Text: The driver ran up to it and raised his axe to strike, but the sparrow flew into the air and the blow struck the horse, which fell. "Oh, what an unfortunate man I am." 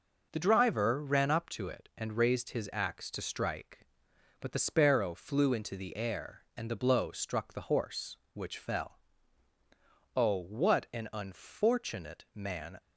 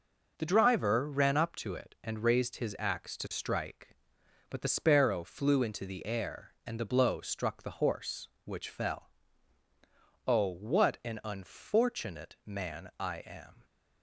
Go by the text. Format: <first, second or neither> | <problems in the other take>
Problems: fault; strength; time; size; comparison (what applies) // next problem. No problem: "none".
second | stops before "I am"; at 12.7 s